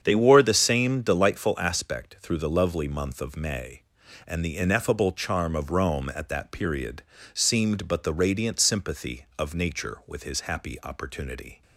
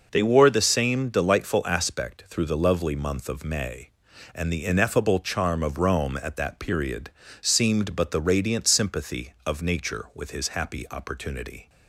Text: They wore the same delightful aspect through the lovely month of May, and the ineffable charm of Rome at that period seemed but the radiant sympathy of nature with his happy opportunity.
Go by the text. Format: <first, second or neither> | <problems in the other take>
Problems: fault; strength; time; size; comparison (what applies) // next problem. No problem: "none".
second | starts louder than the rest; strong; until 1.4 s; 7.5 dB // pauses between "period" and "seemed"; slight; at 7.0 s; 0.30 s long; slight in the second